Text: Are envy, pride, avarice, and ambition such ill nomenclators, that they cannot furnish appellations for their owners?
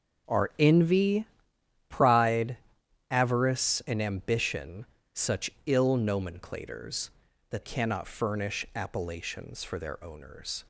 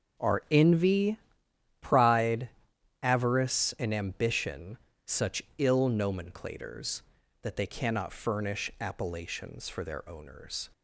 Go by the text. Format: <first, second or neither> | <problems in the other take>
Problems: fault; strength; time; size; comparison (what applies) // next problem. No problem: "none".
second | starts louder than the rest; until 1.9 s; 6.5 dB; also in the second // pauses between "ambition" and "such"; slight; at 4.8 s; 0.28 s long; slight in the second // pauses between "such" and "ill"; slight; at 5.5 s; 0.16 s long; slight in the second // skips "they"; at 7.6 s